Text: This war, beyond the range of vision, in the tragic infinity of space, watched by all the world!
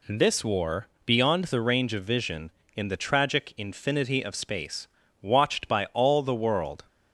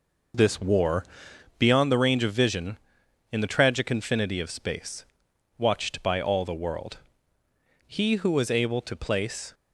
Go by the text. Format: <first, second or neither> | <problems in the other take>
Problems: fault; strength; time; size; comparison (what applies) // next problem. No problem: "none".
first | goes on to say "He who was able to place"; strong; from 7.8 s on; 1.6 s long